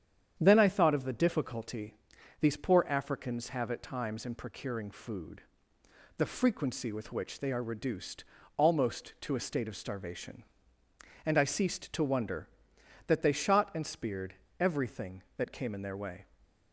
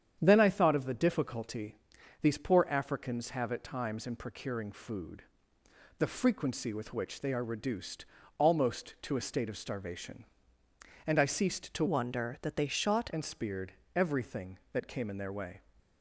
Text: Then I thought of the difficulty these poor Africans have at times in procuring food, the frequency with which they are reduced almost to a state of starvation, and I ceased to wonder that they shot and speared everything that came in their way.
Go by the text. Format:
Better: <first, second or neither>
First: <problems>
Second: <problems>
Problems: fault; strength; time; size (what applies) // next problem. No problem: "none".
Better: first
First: starts louder than the rest; strong; until 1.4 s; 8.5 dB // pauses between "difficulty" and "these"; noticeable; at 1.9 s; 0.46 s long // pauses between "reduced" and "almost"; slight; at 8.2 s; 0.32 s long // pauses between "speared" and "everything"; slight; at 14.3 s; 0.24 s long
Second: starts louder than the rest; strong; until 1.2 s; 8.5 dB // pauses between "difficulty" and "these"; noticeable; at 1.7 s; 0.46 s long // pauses between "reduced" and "almost"; slight; at 8.0 s; 0.32 s long // changes voice from "wonder" to "shot"; from 11.8 to 13.1 s; 1.3 s long // pauses between "speared" and "everything"; slight; at 13.7 s; 0.22 s long